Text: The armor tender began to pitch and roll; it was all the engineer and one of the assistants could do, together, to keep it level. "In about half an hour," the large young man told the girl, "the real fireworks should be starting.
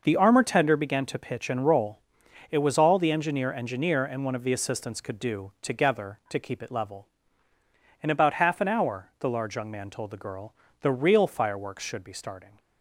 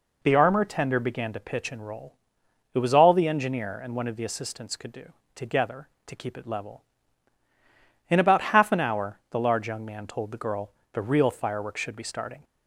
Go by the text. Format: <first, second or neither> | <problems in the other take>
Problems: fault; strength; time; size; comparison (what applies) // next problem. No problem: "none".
second | says "engineer" twice; at 3.5 s